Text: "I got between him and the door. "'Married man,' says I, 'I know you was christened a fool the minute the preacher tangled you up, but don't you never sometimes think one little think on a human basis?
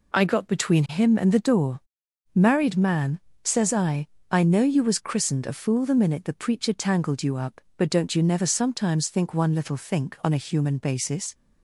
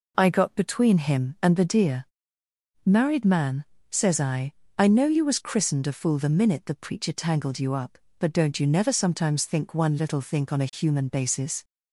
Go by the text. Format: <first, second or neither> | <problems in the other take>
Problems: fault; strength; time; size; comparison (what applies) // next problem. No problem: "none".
first | says "deer" for "door"; at 1.6 s